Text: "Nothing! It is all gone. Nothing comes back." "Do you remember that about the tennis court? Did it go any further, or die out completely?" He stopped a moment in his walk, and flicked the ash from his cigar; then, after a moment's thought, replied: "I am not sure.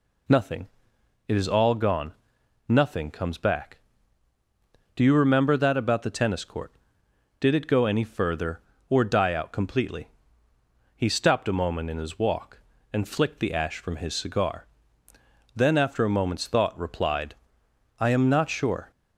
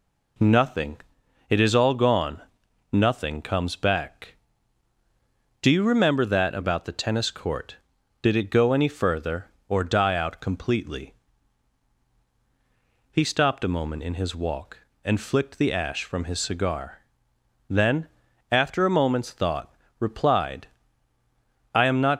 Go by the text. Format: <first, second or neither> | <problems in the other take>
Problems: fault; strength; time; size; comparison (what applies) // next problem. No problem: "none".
first | stops before "sure"; at 22.1 s